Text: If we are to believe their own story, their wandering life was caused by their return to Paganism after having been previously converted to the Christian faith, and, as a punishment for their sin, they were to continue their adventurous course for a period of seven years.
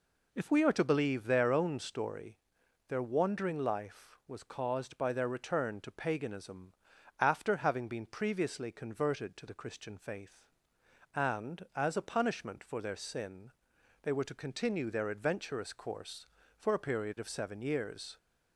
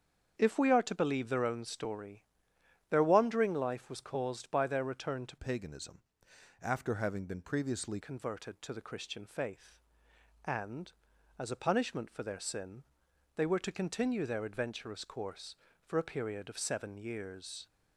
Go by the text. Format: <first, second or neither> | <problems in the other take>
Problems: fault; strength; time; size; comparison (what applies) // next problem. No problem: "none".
first | starts louder than the rest; strong; until 1.3 s; 7.5 dB // changes voice from "Paganism" to "previously"; from 5.3 to 8.0 s; 2.7 s long // pauses between "Paganism" and "after"; noticeable; at 6.0 s; 0.58 s long; noticeable in the first